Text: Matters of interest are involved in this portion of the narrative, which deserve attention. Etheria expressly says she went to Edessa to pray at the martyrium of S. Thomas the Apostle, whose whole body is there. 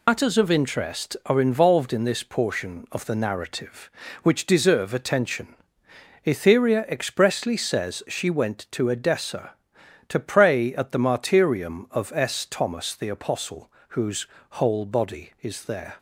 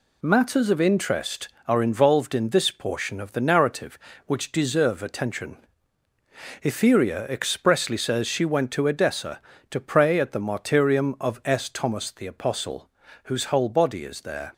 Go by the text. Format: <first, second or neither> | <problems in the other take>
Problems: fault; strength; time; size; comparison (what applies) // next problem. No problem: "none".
second | loses the start of "Matters"; at 0.0 s; 80 ms // pauses between "whose" and "whole"; slight; at 14.2 s; 0.24 s long